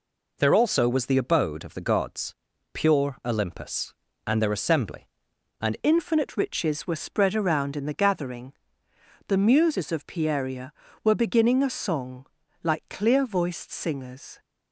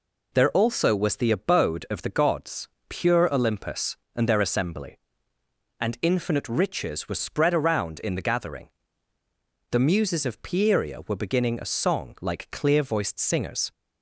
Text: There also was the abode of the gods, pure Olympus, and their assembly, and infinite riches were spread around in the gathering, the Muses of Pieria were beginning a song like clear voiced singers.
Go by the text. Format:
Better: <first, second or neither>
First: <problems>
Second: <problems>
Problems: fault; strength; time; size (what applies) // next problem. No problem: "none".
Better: second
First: changes voice at "infinite"; from 5.8 s on; 8.5 s long // pauses between "song" and "like"; at 12.2 s; 0.38 s long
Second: none